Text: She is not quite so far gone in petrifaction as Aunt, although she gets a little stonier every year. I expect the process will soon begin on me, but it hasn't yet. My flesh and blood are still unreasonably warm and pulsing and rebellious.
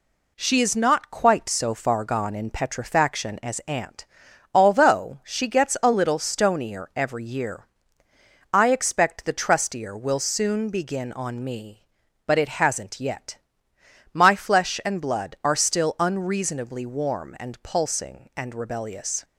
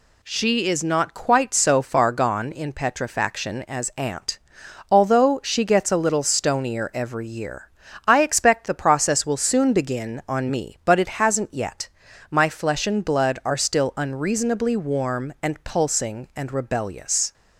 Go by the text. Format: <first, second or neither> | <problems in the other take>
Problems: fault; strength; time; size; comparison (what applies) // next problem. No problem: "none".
second | says "trustier" for "process"; at 9.3 s